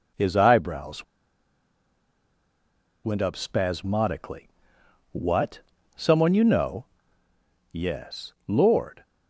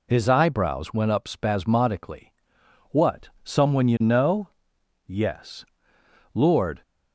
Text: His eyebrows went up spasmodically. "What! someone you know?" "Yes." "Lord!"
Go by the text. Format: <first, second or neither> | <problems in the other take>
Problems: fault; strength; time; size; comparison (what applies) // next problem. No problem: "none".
second | pauses between "eyebrows" and "went"; strong; at 1.0 s; 2.0 s long